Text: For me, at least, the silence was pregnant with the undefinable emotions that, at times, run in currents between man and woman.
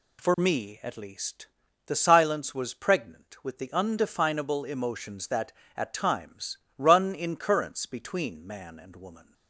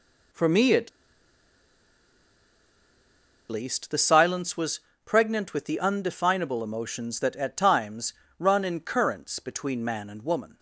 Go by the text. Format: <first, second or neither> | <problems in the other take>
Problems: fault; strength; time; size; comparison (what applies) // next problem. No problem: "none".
first | pauses between "at" and "least"; strong; at 0.8 s; 2.6 s long // pauses between "was" and "pregnant"; slight; at 4.8 s; 0.26 s long